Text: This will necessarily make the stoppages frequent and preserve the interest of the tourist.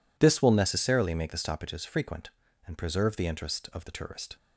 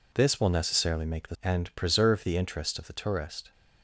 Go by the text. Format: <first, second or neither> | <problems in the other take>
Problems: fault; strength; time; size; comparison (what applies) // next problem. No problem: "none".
first | skips "stoppages frequent"; at 1.3 s